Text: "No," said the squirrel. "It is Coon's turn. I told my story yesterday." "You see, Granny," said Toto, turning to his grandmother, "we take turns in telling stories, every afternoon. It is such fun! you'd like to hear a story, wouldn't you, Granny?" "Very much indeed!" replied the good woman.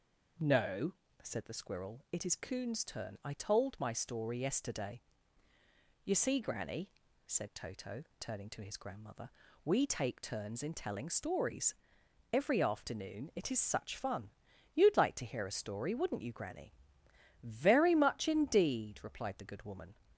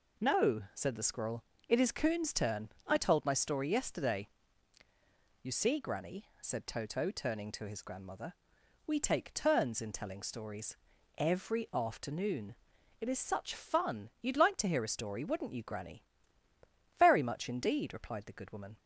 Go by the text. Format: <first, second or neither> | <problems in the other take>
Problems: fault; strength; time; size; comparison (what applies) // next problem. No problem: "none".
neither | none